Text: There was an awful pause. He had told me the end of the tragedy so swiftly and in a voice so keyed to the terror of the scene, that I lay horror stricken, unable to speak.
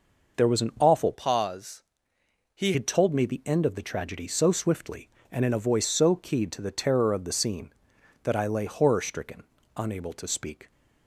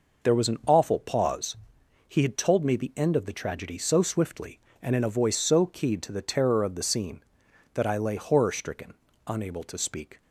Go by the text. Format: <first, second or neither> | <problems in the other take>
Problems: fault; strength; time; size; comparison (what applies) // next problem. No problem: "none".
second | changes voice from "pause" to "He"; from 1.1 to 2.7 s; 1.6 s long